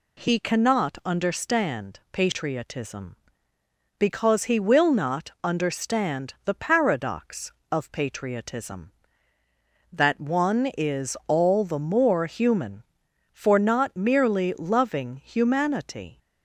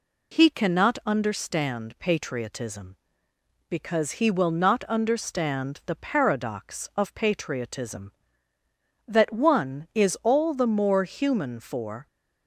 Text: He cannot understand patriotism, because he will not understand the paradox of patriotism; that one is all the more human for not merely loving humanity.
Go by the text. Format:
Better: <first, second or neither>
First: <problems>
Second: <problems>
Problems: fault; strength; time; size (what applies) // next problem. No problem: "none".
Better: first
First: none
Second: stops before "not merely loving humanity"; at 12.0 s